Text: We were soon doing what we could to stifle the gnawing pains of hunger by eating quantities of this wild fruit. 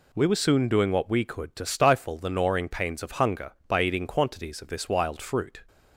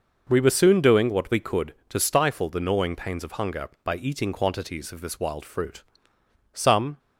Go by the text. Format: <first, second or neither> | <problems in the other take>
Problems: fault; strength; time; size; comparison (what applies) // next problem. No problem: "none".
first | goes on to say "Some"; slight; from 6.5 s on; 0.46 s long